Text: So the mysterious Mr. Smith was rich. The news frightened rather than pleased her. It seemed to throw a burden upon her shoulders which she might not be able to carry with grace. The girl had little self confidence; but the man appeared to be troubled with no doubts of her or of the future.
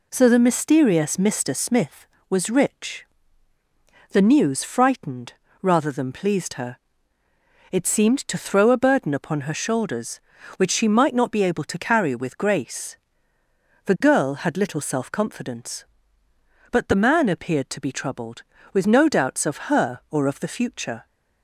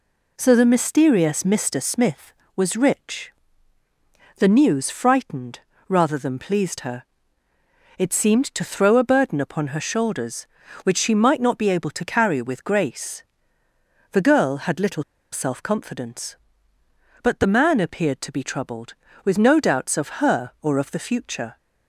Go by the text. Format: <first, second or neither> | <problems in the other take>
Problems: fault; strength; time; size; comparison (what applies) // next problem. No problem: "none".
first | pauses between "frightened" and "rather"; slight; at 5.5 s; 0.28 s long; slight in the first // pauses between "little" and "self"; slight; at 15.0 s; 0.29 s long